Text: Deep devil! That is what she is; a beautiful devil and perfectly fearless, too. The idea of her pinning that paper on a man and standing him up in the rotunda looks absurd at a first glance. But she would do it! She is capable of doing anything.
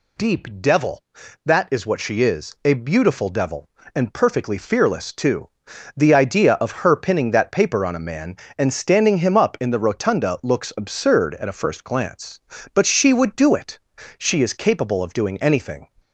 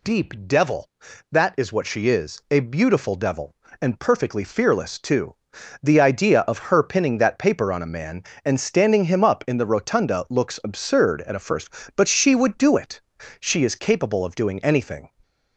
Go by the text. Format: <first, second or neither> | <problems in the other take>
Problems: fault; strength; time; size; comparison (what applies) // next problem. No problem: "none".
first | skips "glance"; at 11.8 s